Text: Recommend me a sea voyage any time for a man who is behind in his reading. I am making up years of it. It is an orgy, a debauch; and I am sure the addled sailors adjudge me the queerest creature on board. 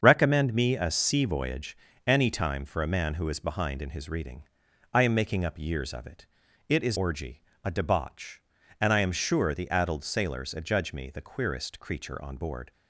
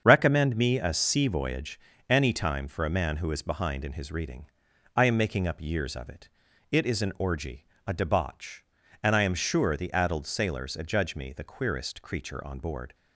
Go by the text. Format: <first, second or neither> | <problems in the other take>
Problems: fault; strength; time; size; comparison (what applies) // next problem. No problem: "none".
second | starts louder than the rest; until 1.0 s; 7 dB; strong in the second // pauses between "voyage" and "any"; slight; at 1.7 s; 0.32 s long; slight in the second // skips "an"; at 6.9 s